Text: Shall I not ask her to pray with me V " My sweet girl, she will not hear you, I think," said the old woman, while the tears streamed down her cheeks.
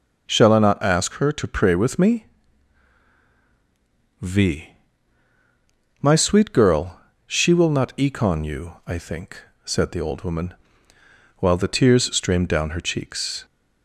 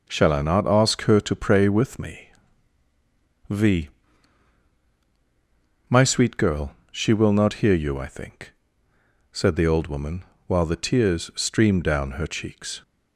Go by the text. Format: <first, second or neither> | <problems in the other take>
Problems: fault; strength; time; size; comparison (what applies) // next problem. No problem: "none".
second | pauses between "me" and "V"; strong; at 2.2 s; 1.9 s long; also in the second // says "econ" for "hear"; at 7.9 s